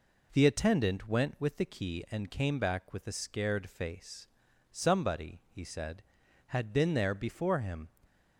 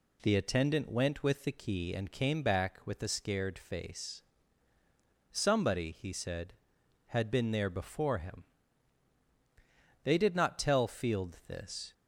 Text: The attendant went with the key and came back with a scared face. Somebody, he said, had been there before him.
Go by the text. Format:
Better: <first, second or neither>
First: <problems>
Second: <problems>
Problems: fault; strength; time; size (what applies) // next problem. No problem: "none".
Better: first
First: none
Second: goes on to say "They did not tell Field this"; strong; from 10.0 s on; 1.9 s long